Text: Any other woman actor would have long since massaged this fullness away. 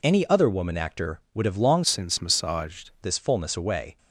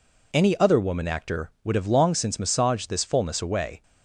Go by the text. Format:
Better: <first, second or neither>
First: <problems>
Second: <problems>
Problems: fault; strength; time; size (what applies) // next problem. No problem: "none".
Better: second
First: changes voice from "since" to "massaged"; from 1.8 to 2.9 s; 1.1 s long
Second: none